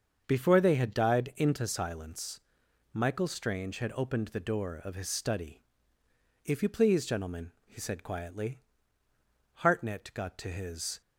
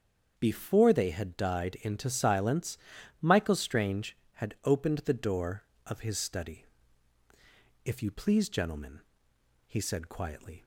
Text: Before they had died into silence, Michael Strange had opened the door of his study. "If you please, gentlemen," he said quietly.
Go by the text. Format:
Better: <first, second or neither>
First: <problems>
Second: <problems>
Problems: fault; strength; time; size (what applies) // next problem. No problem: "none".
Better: second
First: starts louder than the rest; until 1.2 s; 7 dB // goes on to say "Hartnett got to his"; from 9.5 s on; 1.4 s long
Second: starts louder than the rest; strong; until 1.3 s; 7.5 dB